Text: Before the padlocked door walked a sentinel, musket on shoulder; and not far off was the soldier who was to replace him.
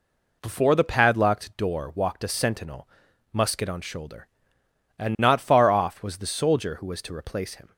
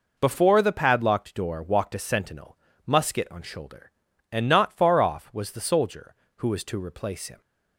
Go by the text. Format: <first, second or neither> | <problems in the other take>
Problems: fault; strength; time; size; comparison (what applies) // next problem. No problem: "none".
neither | none